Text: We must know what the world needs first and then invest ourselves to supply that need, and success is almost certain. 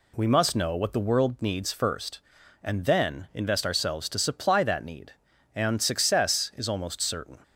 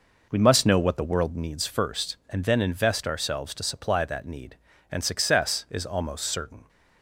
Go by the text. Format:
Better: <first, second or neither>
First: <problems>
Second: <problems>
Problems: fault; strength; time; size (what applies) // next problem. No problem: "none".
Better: first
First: none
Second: starts louder than the rest; noticeable; until 1.5 s; 5 dB